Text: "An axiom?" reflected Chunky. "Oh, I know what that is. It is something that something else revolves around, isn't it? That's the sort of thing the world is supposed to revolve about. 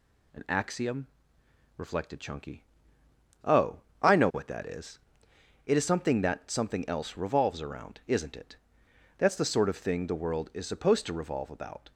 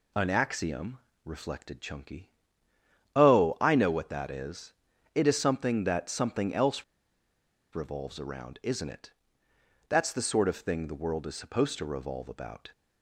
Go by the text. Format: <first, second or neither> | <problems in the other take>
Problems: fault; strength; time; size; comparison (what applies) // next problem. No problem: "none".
first | pauses between "else" and "revolves"; noticeable; at 6.8 s; 0.90 s long